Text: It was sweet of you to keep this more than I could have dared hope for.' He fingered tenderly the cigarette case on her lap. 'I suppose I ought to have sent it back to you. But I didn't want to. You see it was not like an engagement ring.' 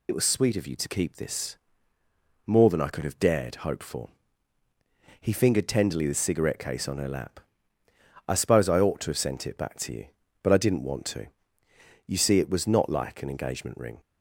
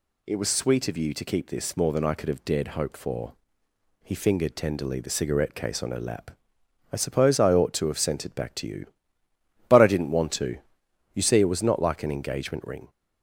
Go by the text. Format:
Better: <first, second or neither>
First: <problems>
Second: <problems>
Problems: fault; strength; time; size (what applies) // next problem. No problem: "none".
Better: second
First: loses the start of "It"; at 0.0 s; 40 ms // pauses between "this" and "more"; noticeable; at 1.5 s; 0.90 s long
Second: none